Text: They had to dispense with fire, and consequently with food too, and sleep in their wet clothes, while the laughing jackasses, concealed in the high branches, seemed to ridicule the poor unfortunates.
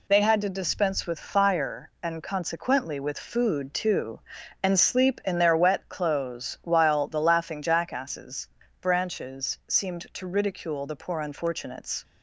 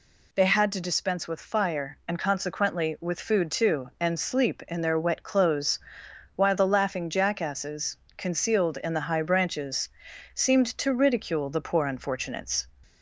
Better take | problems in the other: second | skips "concealed in the high"; at 8.6 s

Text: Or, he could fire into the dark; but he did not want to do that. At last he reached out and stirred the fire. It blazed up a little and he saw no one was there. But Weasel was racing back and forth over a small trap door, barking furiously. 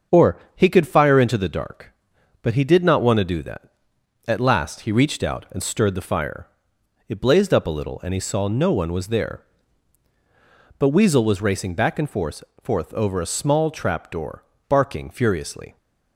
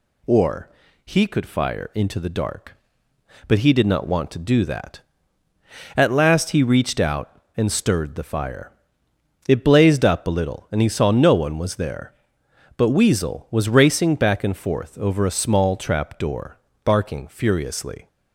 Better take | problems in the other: second | starts louder than the rest; until 1.2 s; 6.5 dB // says "forth" twice; at 12.6 s

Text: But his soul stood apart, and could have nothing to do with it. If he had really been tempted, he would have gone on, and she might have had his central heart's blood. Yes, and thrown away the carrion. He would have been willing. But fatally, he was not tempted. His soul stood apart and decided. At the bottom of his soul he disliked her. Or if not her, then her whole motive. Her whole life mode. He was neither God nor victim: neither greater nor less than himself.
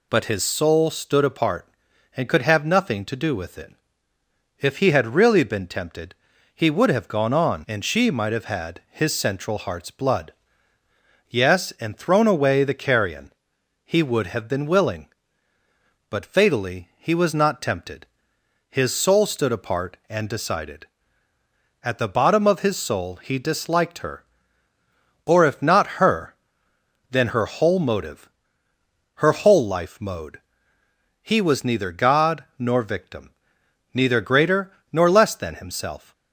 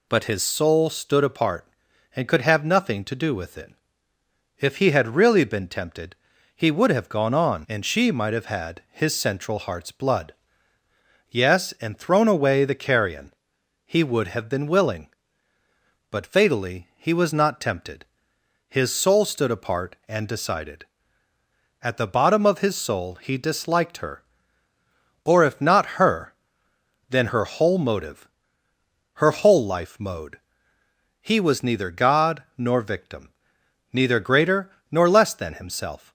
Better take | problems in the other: neither | pauses between "God" and "nor"; slight; the same in both // pauses between "greater" and "nor"; slight; the same in both

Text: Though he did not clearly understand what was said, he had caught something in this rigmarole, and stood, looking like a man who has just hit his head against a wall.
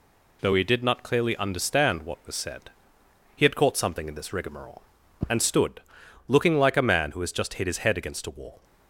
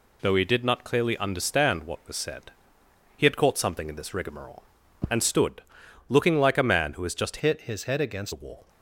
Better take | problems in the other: first | changes voice from "hit" to "against"; from 7.3 to 8.3 s; 1.0 s long

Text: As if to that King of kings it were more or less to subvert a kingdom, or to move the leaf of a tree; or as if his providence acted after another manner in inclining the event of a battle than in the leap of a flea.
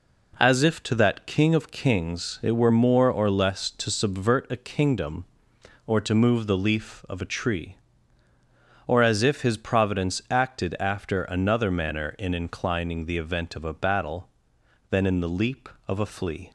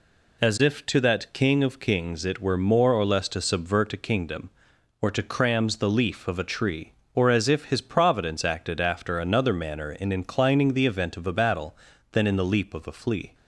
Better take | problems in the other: first | says "crams" for "move"; at 5.2 s

